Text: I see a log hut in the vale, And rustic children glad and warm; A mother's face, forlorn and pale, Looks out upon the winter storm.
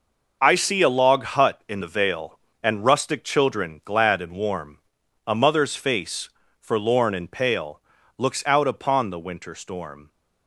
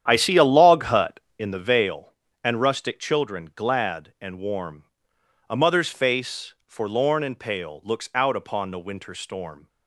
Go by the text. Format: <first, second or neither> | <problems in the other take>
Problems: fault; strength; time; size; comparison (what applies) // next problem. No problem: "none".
first | starts louder than the rest; strong; until 1.5 s; 9.5 dB